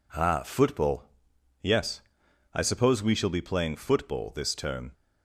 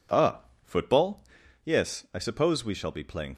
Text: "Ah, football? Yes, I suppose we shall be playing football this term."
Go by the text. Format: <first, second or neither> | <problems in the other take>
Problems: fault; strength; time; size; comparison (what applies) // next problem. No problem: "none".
first | stops before "football this term"; at 3.3 s